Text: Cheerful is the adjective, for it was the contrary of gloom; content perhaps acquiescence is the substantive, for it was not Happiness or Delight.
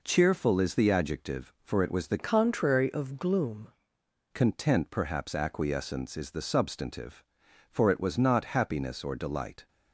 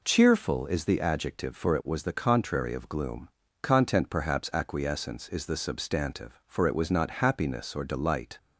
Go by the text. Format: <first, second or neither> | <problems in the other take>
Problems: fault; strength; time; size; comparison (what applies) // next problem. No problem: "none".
second | changes voice from "contrary" to "gloom"; from 2.1 to 3.6 s; 1.5 s long